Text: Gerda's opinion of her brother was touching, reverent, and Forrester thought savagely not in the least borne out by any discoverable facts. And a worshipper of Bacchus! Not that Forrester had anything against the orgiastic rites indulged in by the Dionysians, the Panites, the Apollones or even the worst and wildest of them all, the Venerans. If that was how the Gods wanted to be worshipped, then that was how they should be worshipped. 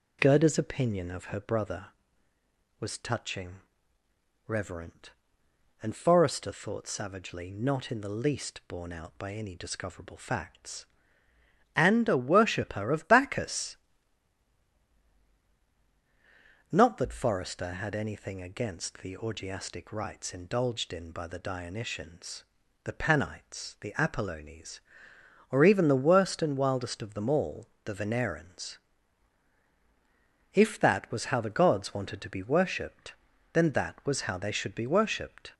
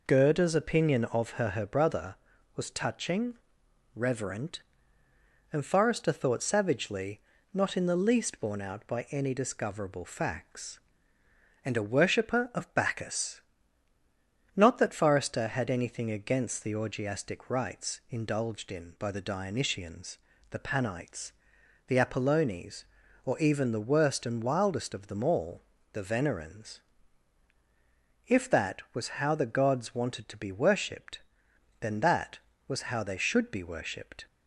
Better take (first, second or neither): first